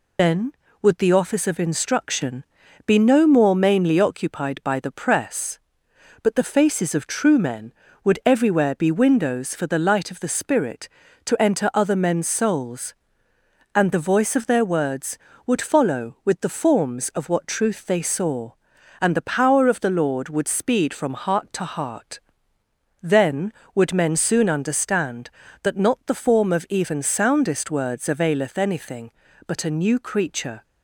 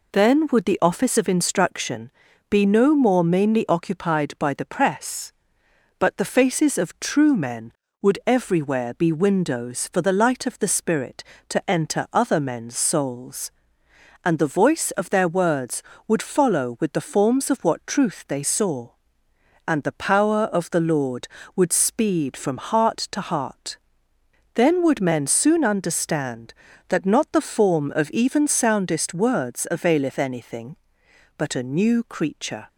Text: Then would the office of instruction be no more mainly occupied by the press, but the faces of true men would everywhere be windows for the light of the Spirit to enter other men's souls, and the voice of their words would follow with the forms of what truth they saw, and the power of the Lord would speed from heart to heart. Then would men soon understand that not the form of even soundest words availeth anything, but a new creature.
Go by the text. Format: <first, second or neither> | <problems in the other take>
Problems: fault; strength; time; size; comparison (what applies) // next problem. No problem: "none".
second | loses the start of "Then"; at 0.1 s; 140 ms // pauses between "instruction" and "be"; at 2.4 s; 0.42 s long; also in the second